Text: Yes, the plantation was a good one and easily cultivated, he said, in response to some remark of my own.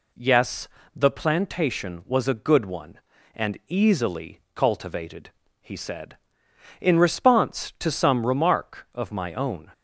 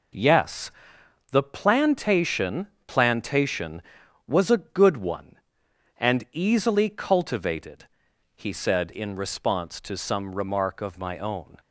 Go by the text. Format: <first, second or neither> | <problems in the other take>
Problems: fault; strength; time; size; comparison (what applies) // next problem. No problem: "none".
first | says "plantation" twice; at 2.8 s